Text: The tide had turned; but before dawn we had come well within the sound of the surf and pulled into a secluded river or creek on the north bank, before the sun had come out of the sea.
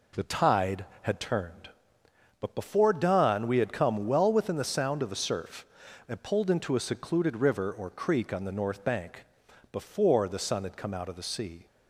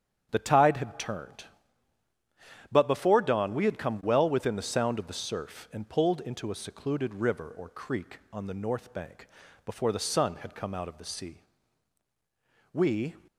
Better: first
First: none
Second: starts louder than the rest; strong; until 1.3 s; 8.5 dB // goes on to say "We"; slight; from 12.7 s on; 0.44 s long

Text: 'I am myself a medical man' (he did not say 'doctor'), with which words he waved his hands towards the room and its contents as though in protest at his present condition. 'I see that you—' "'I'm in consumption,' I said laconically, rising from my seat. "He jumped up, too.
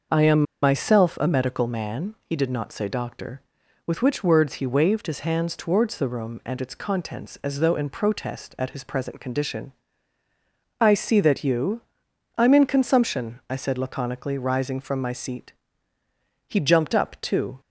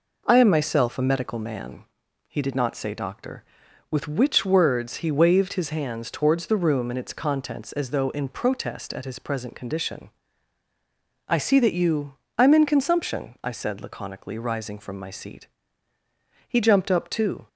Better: second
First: starts louder than the rest; noticeable; until 1.3 s; 6 dB // pauses between "am" and "myself"; slight; at 0.4 s; 0.19 s long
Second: none

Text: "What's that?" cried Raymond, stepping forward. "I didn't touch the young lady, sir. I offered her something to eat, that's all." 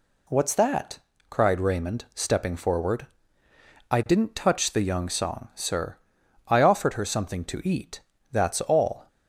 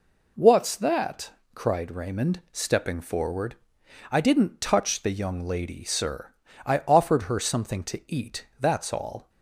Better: second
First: says "song" for "lady"; at 5.0 s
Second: none

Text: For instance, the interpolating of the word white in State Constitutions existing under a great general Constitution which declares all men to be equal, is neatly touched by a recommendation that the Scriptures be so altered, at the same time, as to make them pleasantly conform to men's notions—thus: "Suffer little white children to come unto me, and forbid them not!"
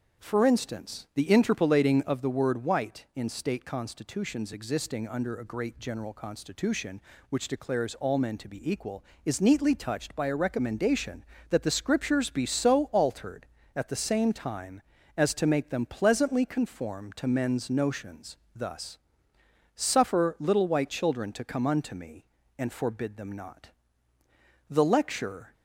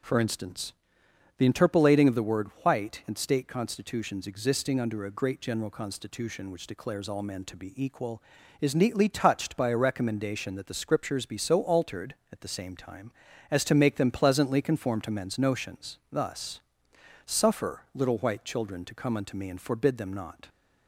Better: second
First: goes on to say "The lecture"; noticeable; from 24.6 s on; 0.84 s long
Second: none

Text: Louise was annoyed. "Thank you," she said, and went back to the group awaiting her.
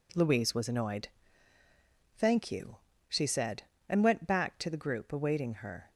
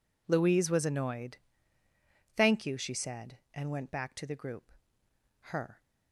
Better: first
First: none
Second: skips "awaiting"; at 5.1 s

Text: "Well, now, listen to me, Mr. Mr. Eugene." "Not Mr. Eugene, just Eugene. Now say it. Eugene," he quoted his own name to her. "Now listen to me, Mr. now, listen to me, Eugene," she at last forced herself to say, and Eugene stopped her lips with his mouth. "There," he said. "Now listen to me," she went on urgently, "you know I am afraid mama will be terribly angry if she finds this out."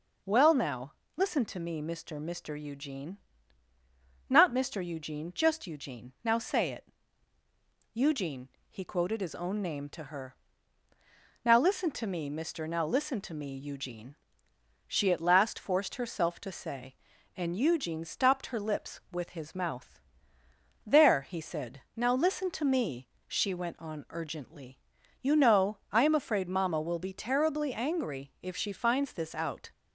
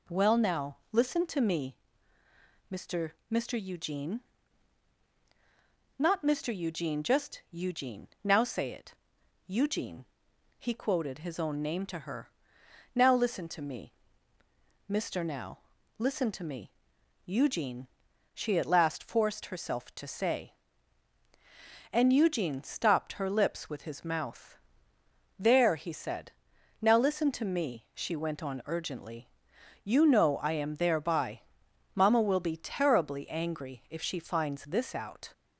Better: first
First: none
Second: says "thereby" for "afraid"; at 30.7 s

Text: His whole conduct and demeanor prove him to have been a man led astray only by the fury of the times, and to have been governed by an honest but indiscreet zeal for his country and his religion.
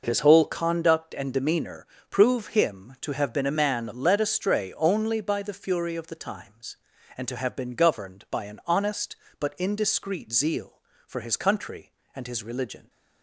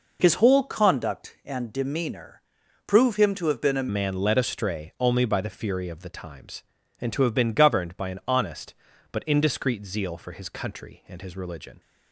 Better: first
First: pauses between "demeanor" and "prove"; slight; at 1.8 s; 0.24 s long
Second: pauses between "demeanor" and "prove"; at 2.4 s; 0.42 s long // changes voice at "man"; from 3.8 s on; 7.9 s long

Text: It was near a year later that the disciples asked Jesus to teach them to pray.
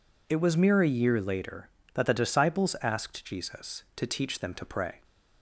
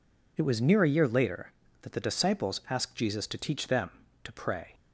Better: second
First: says "mere" for "near"; at 0.5 s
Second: none

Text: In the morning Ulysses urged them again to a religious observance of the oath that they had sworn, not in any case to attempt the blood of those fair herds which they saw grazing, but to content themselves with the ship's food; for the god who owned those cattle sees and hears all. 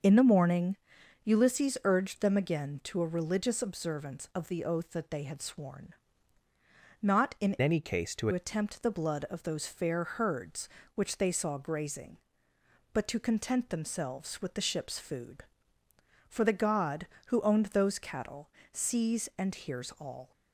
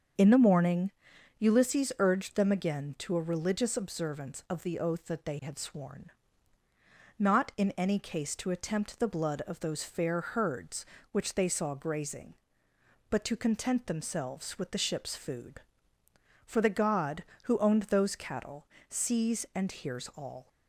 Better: second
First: starts louder than the rest; until 1.5 s; 6.5 dB // pauses between "morning" and "Ulysses"; noticeable; at 0.7 s; 0.48 s long // changes voice from "any" to "to"; from 7.6 to 8.2 s; 0.6 s long // pauses between "cattle" and "sees"; slight; at 18.4 s; 0.24 s long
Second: starts louder than the rest; strong; until 1.6 s; 7 dB // pauses between "morning" and "Ulysses"; noticeable; at 0.9 s; 0.48 s long // pauses between "cattle" and "sees"; slight; at 18.6 s; 0.24 s long

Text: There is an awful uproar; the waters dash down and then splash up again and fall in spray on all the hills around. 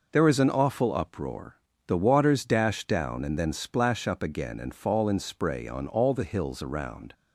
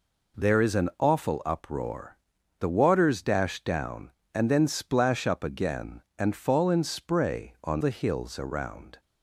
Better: first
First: none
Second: skips "all"; at 7.8 s

